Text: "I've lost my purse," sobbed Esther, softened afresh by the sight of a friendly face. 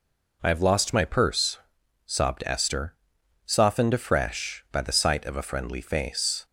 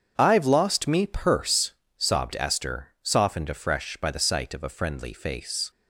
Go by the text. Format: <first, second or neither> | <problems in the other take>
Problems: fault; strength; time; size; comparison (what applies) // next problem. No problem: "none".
first | starts louder than the rest; strong; until 1.1 s; 7.5 dB // says "me" for "my"; at 0.8 s